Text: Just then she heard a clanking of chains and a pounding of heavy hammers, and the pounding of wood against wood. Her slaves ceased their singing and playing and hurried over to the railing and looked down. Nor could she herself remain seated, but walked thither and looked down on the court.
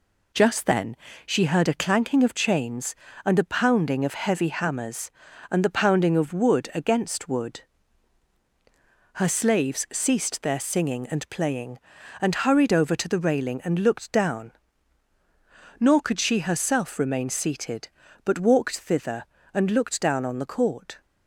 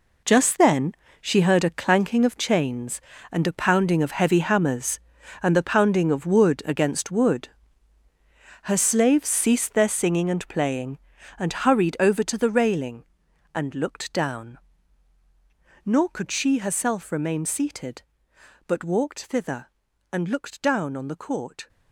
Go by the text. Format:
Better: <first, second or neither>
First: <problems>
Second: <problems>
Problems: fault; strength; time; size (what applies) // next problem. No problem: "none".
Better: first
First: pauses between "then" and "she"; slight; at 0.9 s; 0.30 s long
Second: gets quieter; strong; throughout; 11.5 dB // pauses between "then" and "she"; slight; at 0.9 s; 0.26 s long